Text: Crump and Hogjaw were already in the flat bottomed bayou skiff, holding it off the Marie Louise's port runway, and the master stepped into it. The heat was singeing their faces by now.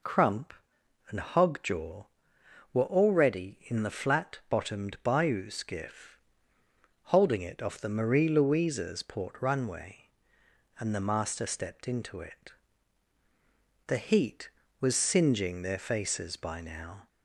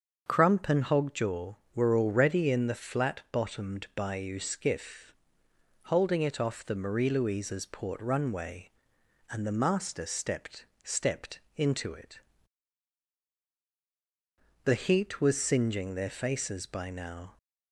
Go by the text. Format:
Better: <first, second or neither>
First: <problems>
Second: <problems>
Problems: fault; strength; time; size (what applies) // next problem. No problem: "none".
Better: first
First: none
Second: starts louder than the rest; until 1.2 s; 7 dB // says "stepped" twice; at 10.8 s